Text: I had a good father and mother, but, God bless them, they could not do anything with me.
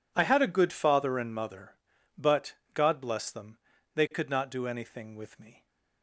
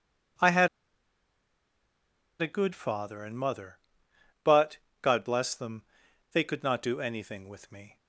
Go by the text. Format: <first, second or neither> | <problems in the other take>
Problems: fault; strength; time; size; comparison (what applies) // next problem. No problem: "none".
first | pauses between "had" and "a"; strong; at 0.6 s; 1.7 s long